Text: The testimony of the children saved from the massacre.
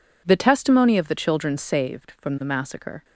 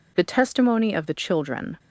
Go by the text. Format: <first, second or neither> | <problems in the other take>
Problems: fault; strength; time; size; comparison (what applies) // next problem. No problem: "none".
first | stops before "saved from the massacre"; at 1.7 s